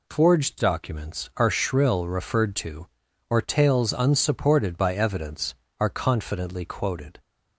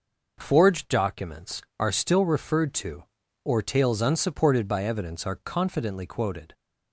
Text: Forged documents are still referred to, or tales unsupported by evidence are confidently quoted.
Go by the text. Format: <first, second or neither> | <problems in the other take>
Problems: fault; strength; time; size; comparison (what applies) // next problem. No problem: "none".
second | says "shrill" for "still"; at 1.4 s